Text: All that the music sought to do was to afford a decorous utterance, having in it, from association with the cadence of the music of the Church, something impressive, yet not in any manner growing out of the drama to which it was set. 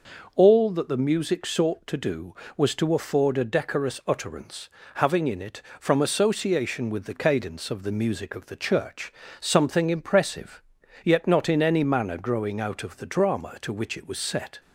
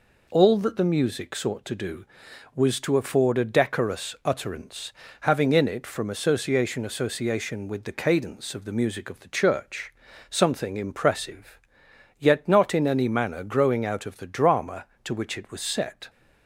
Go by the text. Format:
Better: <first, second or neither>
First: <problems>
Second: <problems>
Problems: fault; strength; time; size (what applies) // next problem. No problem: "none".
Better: first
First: none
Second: says "association" twice; at 6.8 s